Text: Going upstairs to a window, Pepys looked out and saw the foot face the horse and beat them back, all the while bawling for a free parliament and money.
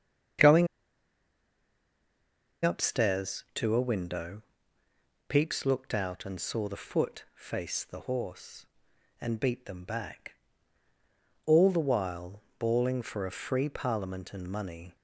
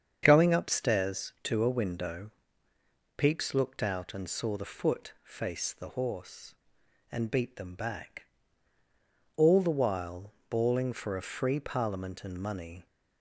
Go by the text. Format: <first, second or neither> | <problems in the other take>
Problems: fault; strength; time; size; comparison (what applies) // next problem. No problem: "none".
second | starts louder than the rest; strong; until 3.3 s; 7.5 dB; strong in the second // pauses between "Going" and "upstairs"; strong; at 0.6 s; 1.9 s long // pauses between "while" and "bawling"; slight; at 12.4 s; 0.18 s long; slight in the second